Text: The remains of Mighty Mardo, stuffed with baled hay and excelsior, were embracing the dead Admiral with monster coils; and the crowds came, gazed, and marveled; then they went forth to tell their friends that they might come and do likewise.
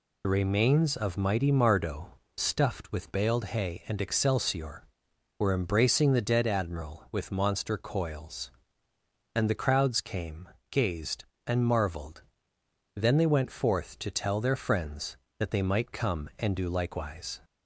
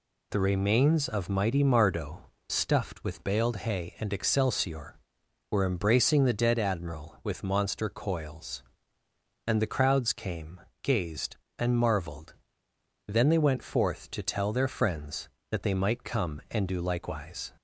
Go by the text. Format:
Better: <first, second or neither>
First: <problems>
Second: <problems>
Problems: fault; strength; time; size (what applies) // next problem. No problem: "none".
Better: second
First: loses the start of "The"; at 0.2 s; 50 ms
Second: none